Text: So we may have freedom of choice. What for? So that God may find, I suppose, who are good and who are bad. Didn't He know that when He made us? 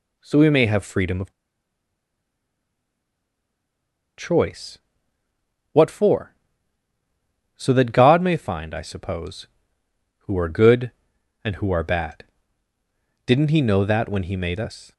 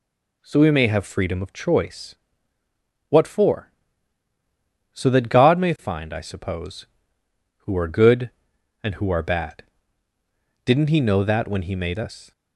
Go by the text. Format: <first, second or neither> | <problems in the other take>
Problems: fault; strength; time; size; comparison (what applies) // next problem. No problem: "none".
second | pauses between "of" and "choice"; strong; at 1.3 s; 2.8 s long